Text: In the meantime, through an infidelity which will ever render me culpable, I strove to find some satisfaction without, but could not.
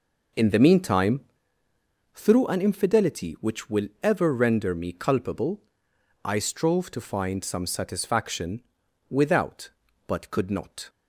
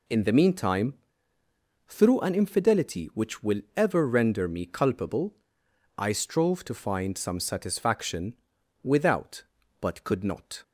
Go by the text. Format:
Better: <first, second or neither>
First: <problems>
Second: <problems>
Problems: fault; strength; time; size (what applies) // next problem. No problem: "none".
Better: second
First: starts louder than the rest; noticeable; until 1.6 s; 5 dB // pauses between "satisfaction" and "without"; noticeable; at 8.6 s; 0.50 s long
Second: pauses between "satisfaction" and "without"; noticeable; at 8.3 s; 0.50 s long